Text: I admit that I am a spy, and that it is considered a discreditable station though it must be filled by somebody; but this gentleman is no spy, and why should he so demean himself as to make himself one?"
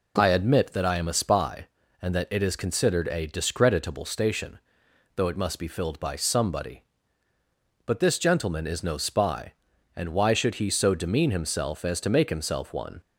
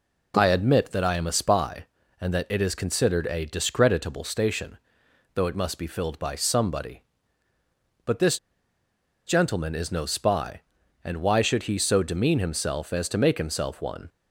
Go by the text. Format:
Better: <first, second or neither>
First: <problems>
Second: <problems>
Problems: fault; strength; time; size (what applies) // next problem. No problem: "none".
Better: first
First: pauses between "station" and "though"; noticeable; at 4.5 s; 0.58 s long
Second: pauses between "station" and "though"; noticeable; at 4.7 s; 0.58 s long // pauses between "this" and "gentleman"; noticeable; at 8.3 s; 0.89 s long